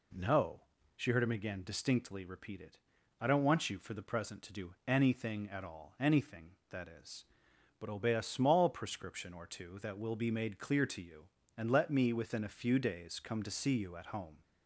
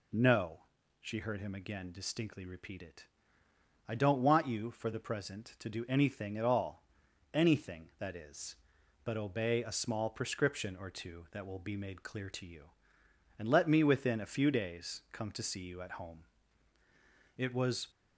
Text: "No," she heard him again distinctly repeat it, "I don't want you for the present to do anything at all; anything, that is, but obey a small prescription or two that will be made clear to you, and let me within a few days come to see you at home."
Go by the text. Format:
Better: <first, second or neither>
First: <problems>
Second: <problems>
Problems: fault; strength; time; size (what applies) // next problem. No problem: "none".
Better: first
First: none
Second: goes on to say "It was"; from 17.3 s on; 0.52 s long